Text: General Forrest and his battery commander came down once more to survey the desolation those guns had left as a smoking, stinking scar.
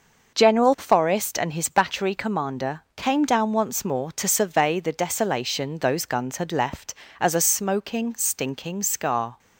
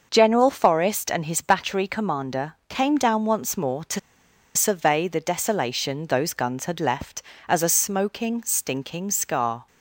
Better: first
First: starts louder than the rest; noticeable; until 1.3 s; 6 dB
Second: starts louder than the rest; noticeable; until 1.1 s; 6 dB // pauses between "to" and "survey"; noticeable; at 3.9 s; 0.56 s long

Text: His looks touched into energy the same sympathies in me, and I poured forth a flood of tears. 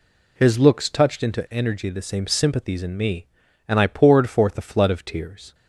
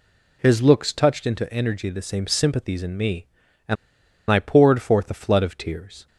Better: first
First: none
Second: pauses between "and" and "I"; noticeable; at 3.7 s; 0.54 s long

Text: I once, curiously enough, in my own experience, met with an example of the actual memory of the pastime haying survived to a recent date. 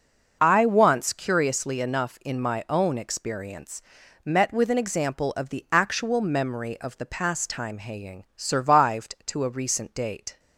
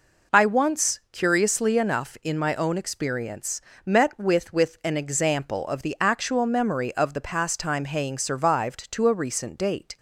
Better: first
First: none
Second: says "with" twice; at 4.5 s

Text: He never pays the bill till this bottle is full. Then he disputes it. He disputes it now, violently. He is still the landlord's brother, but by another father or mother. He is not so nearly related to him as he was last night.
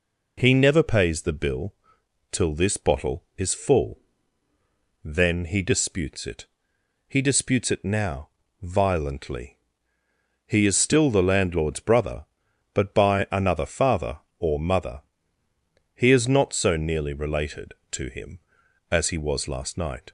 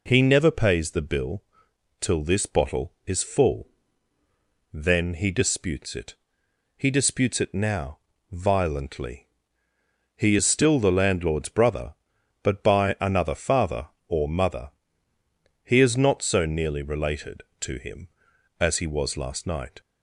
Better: neither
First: pauses between "bill" and "till"; noticeable; at 1.7 s; 0.56 s long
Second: pauses between "bill" and "till"; noticeable; at 1.4 s; 0.56 s long

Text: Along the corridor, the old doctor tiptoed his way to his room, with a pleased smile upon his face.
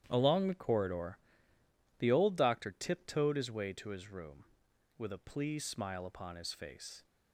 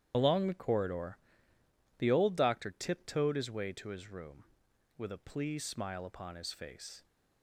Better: first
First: starts louder than the rest; strong; until 1.0 s; 10.5 dB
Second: loses the start of "Along"; at 0.1 s; 115 ms // starts louder than the rest; strong; until 1.1 s; 10.5 dB

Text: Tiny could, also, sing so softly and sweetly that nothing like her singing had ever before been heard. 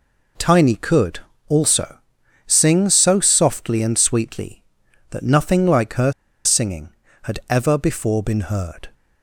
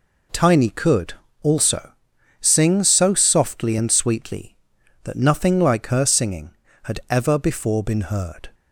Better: second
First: pauses between "her" and "singing"; slight; at 6.1 s; 0.32 s long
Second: none

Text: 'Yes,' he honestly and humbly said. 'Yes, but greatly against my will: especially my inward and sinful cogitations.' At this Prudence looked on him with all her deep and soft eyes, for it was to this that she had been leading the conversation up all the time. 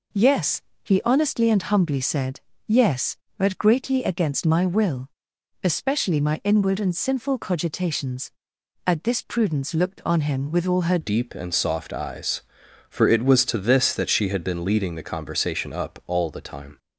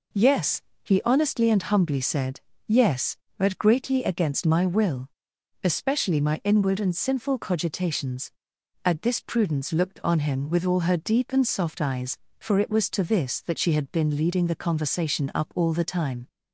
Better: second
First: changes voice at "deep"; from 11.0 s on; 5.7 s long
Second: none

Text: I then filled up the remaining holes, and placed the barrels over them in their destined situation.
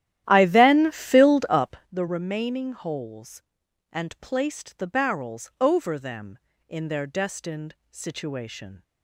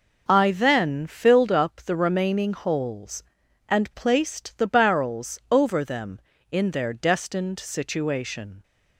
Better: second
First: starts louder than the rest; strong; until 1.9 s; 12.5 dB // pauses between "up" and "the"; slight; at 1.7 s; 0.16 s long // pauses between "destined" and "situation"; slight; at 7.7 s; 0.16 s long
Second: none

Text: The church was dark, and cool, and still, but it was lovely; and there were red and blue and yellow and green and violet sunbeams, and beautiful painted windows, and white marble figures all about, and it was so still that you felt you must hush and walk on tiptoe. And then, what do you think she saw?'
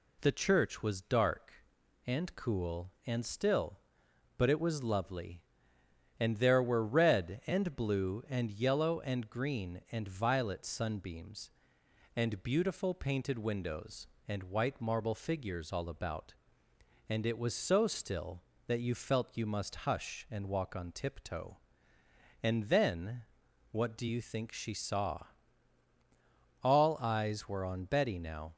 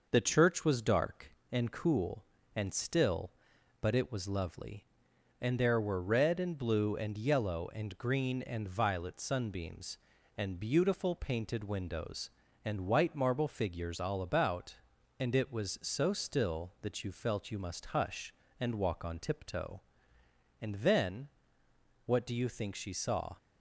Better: second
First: goes on to say "All eyes were on Betty now"; strong; from 26.6 s on; 1.9 s long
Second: none

